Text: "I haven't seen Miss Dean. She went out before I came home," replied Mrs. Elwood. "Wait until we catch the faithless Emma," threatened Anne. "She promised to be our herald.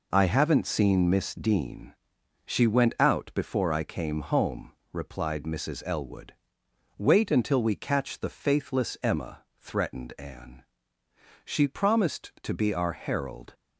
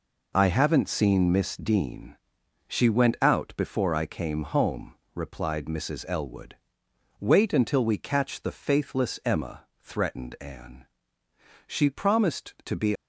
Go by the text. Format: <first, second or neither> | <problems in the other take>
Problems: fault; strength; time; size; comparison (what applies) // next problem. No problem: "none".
first | stops before "our herald"; at 12.9 s